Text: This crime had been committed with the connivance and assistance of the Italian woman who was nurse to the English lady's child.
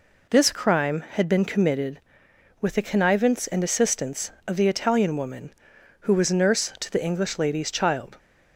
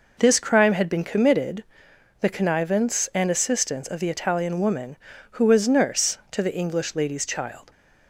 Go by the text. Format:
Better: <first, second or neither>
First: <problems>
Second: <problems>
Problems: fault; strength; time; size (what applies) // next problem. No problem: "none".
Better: first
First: none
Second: skips "with"; at 1.9 s